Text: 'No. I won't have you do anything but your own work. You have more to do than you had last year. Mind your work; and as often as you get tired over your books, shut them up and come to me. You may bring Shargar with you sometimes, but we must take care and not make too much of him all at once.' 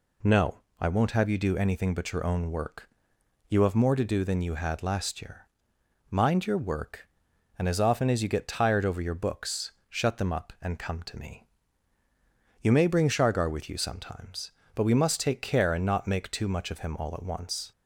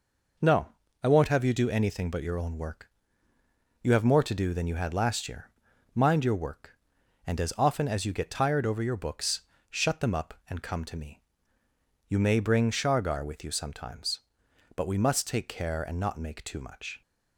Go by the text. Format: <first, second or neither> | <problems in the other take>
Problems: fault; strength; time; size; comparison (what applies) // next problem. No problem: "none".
first | stops before "of him all at once"; at 17.0 s